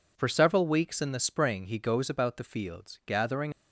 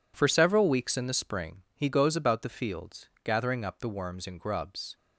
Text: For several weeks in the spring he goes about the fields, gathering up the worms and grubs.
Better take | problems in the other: second | stops before "up the worms and grubs"; at 3.5 s

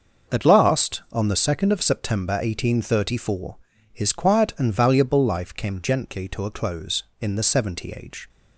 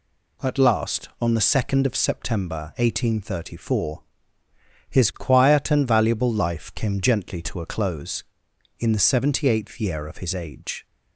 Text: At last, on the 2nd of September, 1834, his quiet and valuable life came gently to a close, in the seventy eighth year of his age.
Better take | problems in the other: second | starts louder than the rest; noticeable; until 1.3 s; 6 dB // skips "eighth year of his"; at 7.9 s

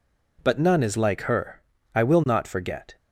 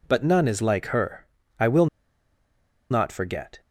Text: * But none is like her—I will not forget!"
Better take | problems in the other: first | pauses between "will" and "not"; at 1.8 s; 1.0 s long

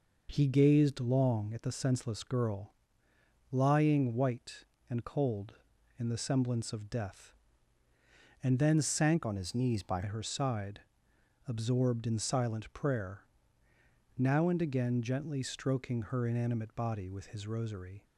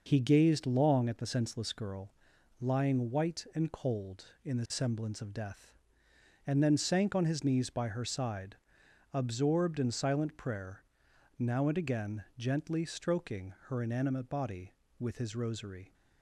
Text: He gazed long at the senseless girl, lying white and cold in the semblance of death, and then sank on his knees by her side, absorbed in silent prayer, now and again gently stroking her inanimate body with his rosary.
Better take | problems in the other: second | changes voice from "on" to "by"; from 9.2 to 10.0 s; 0.8 s long

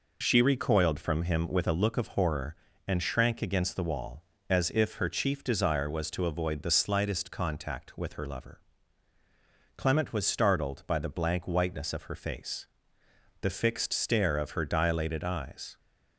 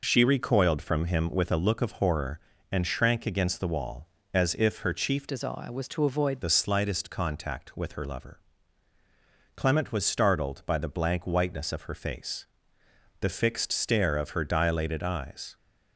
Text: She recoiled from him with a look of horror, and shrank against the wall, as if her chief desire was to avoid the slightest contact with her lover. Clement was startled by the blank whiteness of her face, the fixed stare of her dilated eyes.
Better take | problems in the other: first | changes voice from "desire" to "avoid"; from 5.2 to 6.4 s; 1.2 s long

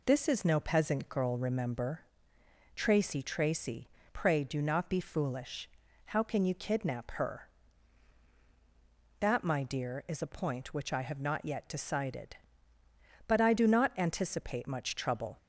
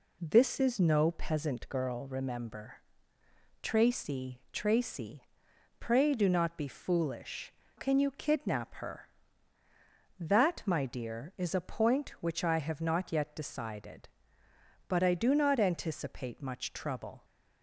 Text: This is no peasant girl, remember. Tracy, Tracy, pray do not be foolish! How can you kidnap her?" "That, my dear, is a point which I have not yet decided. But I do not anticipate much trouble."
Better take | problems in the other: first | skips "How"; at 7.6 s

